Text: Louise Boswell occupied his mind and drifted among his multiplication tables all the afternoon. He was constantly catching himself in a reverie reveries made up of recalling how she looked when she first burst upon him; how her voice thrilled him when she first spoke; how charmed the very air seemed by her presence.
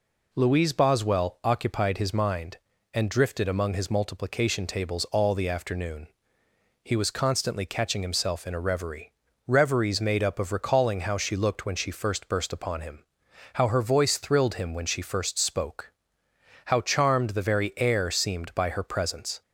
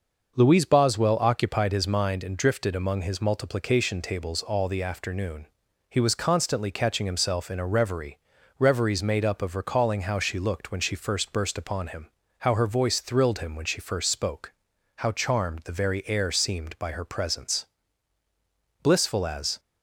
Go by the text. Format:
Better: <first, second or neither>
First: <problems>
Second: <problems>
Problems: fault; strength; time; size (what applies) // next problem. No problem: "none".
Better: first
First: pauses between "reverie" and "reveries"; slight; at 9.1 s; 0.34 s long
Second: starts louder than the rest; noticeable; until 1.3 s; 6 dB // pauses between "reverie" and "reveries"; at 8.1 s; 0.42 s long // goes on to say "Blissful as"; noticeable; from 18.8 s on; 0.76 s long